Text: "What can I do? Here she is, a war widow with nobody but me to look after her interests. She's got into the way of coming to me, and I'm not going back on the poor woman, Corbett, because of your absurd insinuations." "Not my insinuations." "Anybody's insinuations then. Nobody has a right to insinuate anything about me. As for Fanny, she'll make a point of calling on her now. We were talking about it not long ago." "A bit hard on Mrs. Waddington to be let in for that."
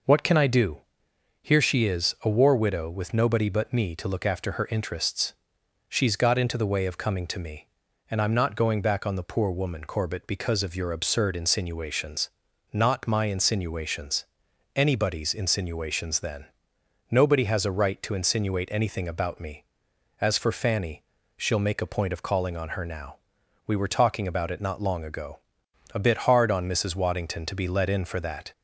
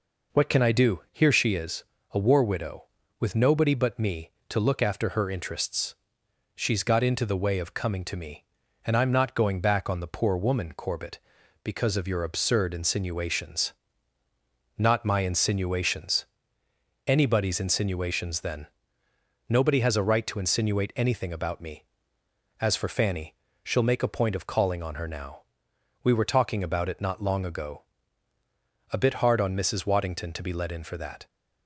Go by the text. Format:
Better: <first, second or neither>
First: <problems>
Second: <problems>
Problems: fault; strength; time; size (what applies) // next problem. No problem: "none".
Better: neither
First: none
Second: none